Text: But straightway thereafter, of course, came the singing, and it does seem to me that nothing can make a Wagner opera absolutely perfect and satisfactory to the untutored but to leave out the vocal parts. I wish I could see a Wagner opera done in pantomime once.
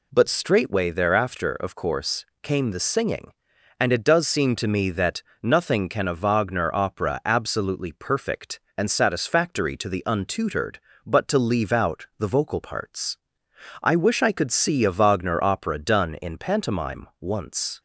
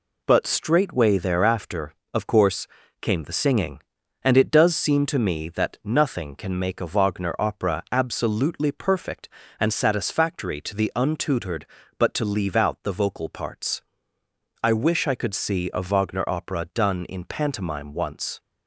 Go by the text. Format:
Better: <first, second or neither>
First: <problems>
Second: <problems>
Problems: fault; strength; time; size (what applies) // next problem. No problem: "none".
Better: second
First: pauses between "that" and "nothing"; slight; at 5.2 s; 0.20 s long // skips "make"; at 6.0 s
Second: none